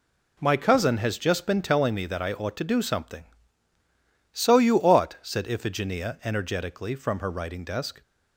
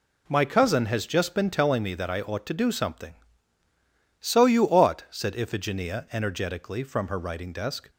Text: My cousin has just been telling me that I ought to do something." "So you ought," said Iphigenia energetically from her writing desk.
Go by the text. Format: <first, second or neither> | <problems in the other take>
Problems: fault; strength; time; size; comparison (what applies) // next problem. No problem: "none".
neither | none